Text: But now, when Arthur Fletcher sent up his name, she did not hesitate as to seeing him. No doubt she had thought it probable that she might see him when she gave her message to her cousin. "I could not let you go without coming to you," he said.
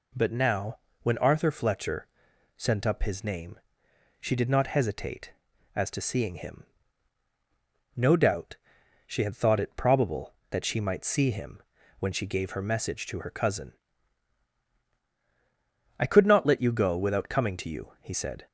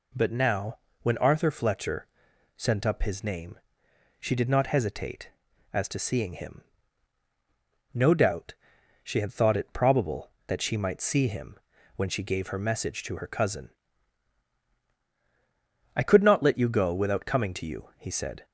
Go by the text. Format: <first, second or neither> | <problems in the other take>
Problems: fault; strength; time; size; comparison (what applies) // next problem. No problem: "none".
neither | pauses between "Fletcher" and "sent"; noticeable; the same in both // pauses between "doubt" and "she"; noticeable; the same in both // pauses between "him" and "when"; the same in both